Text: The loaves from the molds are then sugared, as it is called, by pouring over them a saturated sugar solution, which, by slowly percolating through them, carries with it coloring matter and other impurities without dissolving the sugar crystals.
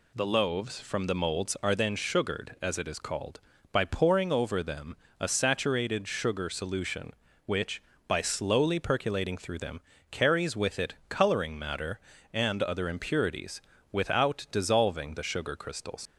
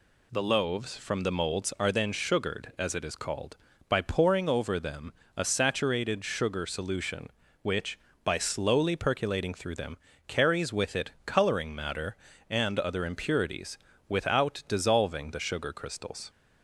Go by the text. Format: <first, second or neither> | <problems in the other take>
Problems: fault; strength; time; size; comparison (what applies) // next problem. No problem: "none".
second | pauses between "them" and "a"; slight; at 4.9 s; 0.24 s long; slight in the second // pauses between "it" and "coloring"; slight; at 10.9 s; 0.16 s long; slight in the second // pauses between "impurities" and "without"; slight; at 13.5 s; 0.32 s long; slight in the second // leaves "crystals" unfinished; at 16.0 s; 75 ms